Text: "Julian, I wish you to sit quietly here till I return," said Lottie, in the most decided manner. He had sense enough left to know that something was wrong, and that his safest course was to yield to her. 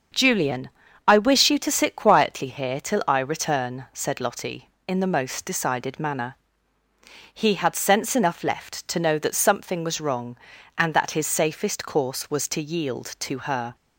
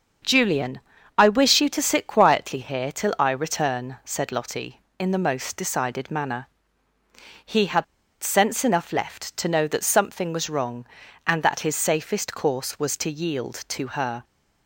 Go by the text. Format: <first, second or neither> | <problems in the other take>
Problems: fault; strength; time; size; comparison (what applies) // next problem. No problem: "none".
first | starts louder than the rest; until 1.6 s; 7 dB; also in the first // pauses between "had" and "sense"; at 7.8 s; 0.38 s long